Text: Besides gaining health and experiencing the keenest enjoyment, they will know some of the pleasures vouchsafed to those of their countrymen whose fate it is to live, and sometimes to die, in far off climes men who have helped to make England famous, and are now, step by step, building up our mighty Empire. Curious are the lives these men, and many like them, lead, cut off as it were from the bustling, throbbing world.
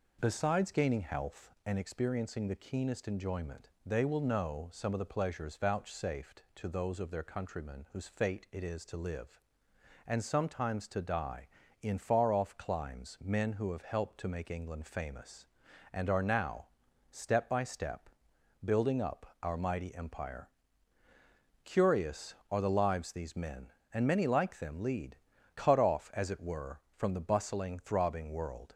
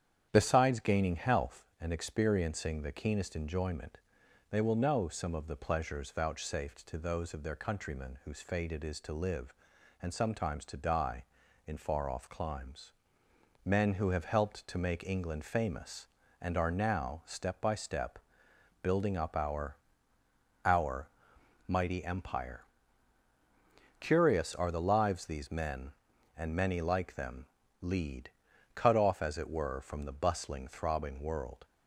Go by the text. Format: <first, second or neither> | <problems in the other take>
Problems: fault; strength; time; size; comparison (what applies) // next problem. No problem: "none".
first | starts louder than the rest; strong; until 1.3 s; 9 dB // pauses between "climes" and "men"; noticeable; at 12.9 s; 0.70 s long // says "our" twice; at 20.6 s